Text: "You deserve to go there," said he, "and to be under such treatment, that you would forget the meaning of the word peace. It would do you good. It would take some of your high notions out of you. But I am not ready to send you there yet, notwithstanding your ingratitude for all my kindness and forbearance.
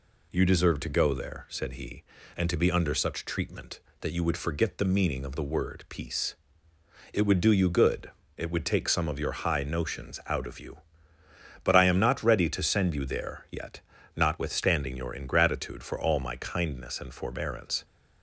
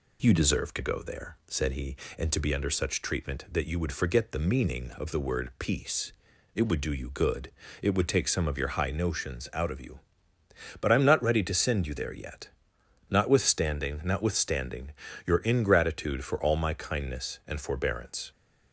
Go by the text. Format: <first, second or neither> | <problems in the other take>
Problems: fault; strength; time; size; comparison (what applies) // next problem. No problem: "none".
first | says "notwithstanding" twice; at 14.0 s